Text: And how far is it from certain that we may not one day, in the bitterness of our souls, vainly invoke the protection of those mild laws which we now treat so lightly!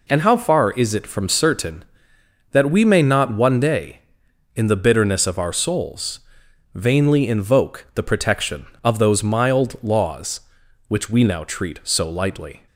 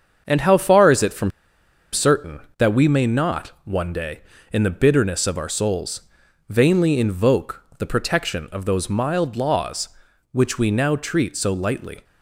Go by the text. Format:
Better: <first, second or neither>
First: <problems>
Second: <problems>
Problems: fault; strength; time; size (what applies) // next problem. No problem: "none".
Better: first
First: none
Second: starts louder than the rest; until 1.2 s; 7 dB // pauses between "from" and "certain"; noticeable; at 1.3 s; 0.62 s long